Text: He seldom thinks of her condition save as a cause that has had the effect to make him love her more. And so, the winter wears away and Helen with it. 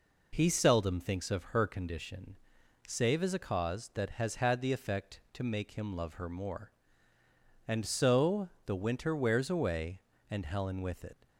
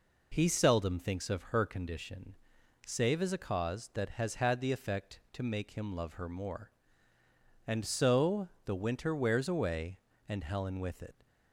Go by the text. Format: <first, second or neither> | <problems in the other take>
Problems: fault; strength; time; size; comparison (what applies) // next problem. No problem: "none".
neither | pauses between "condition" and "save"; noticeable; the same in both